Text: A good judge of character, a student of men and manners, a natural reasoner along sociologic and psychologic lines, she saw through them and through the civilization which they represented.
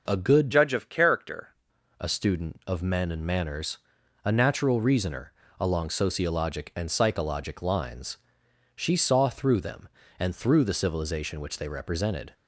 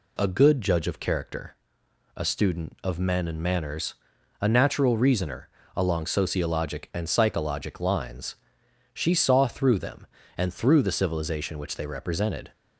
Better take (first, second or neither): second